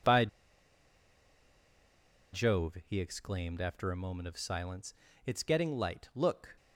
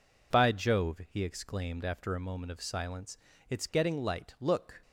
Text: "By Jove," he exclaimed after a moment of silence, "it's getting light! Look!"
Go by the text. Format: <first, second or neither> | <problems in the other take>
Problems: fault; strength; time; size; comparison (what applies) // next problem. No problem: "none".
second | pauses between "By" and "Jove"; strong; at 0.2 s; 2.0 s long